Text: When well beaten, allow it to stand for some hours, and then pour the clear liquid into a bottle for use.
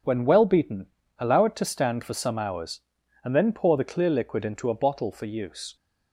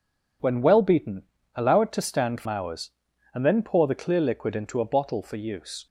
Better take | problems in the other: first | skips "some"; at 2.4 s

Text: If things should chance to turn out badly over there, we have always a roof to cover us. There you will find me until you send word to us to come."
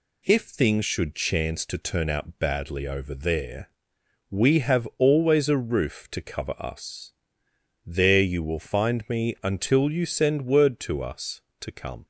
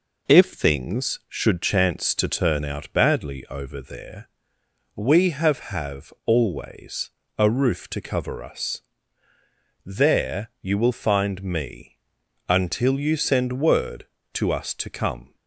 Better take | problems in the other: first | says "have" twice; at 5.6 s // pauses between "always" and "a"; slight; at 7.1 s; 0.26 s long // pauses between "me" and "until"; noticeable; at 11.9 s; 0.52 s long

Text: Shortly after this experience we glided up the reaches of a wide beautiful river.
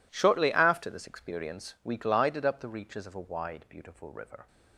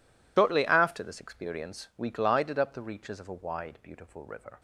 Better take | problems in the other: first | loses the start of "Shortly"; at 0.3 s; 125 ms

